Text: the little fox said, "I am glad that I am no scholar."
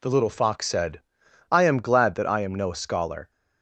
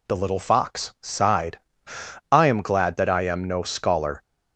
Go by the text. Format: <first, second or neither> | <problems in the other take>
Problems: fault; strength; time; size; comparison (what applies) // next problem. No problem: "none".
first | says "sighed" for "said"; at 1.0 s